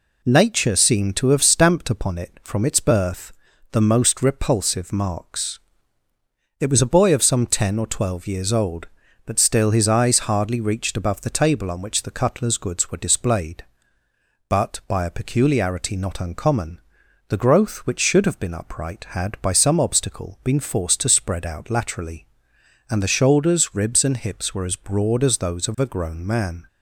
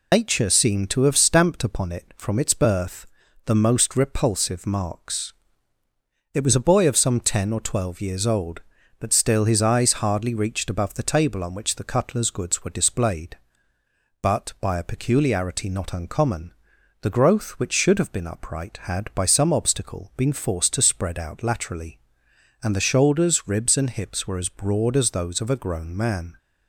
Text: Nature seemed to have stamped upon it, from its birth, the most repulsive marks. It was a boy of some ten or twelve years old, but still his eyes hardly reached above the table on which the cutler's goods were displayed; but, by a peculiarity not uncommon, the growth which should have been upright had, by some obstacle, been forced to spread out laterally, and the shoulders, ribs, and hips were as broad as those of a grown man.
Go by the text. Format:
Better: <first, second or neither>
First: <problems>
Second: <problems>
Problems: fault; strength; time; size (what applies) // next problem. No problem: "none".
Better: first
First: none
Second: loses the start of "Nature"; at 0.1 s; 140 ms